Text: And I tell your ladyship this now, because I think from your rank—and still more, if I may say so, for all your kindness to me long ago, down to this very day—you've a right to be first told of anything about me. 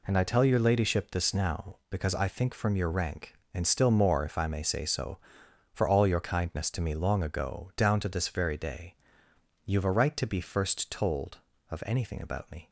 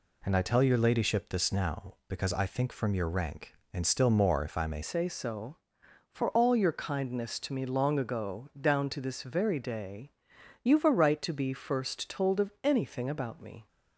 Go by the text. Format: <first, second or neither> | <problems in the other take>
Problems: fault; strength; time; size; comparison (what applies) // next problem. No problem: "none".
first | changes voice at "say"; from 4.8 s on; 8.8 s long